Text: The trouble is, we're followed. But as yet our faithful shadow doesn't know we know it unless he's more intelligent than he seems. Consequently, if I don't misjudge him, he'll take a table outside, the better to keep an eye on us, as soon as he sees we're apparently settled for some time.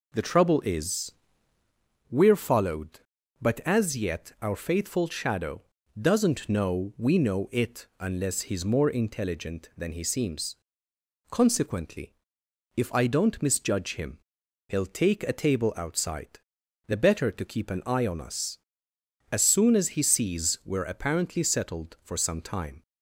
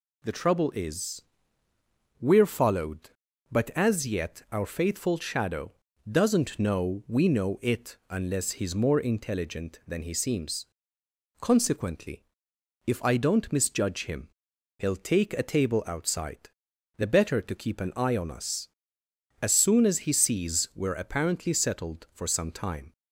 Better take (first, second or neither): second